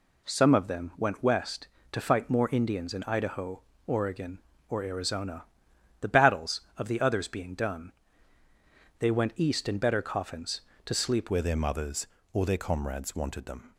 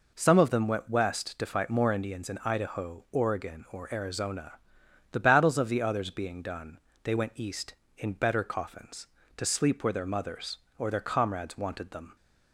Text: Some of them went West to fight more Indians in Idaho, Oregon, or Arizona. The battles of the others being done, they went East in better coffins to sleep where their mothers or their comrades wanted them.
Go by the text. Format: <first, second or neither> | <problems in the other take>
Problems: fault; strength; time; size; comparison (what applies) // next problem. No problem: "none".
second | changes voice at "where"; from 11.3 s on; 2.4 s long